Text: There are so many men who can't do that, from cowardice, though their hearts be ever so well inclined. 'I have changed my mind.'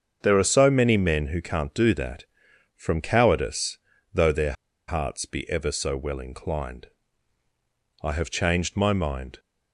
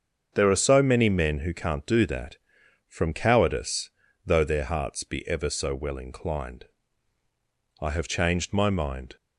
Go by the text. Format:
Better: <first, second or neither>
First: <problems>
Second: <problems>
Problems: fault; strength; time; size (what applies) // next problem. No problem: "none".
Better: second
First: starts louder than the rest; until 1.2 s; 7 dB // pauses between "their" and "hearts"; slight; at 4.5 s; 0.35 s long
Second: starts louder than the rest; until 1.3 s; 7 dB